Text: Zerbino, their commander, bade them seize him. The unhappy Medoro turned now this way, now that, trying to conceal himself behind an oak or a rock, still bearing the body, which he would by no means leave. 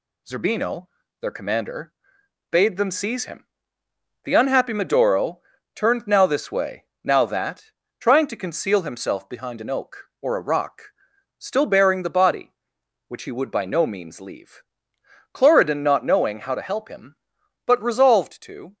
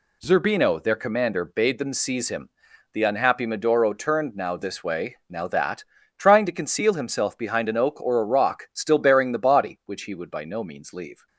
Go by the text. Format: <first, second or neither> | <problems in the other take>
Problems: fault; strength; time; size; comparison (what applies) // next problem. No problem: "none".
second | pauses between "Medoro" and "turned"; slight; at 5.3 s; 0.36 s long // goes on to say "Cloridan not knowing how to help him but resolved to"; strong; from 15.3 s on; 3.4 s long